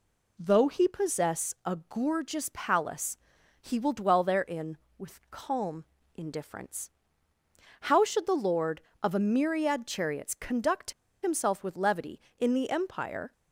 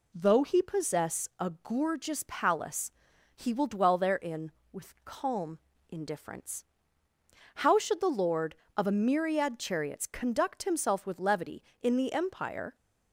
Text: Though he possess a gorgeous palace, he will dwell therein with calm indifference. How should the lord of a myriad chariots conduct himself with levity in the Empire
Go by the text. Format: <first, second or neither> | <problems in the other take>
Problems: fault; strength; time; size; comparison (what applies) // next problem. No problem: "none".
second | pauses between "calm" and "indifference"; slight; at 5.8 s; 0.30 s long; slight in the second // pauses between "conduct" and "himself"; slight; at 10.9 s; 0.31 s long